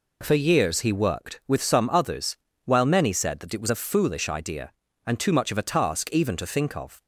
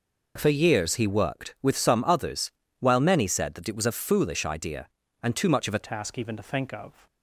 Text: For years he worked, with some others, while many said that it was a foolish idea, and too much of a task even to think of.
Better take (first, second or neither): first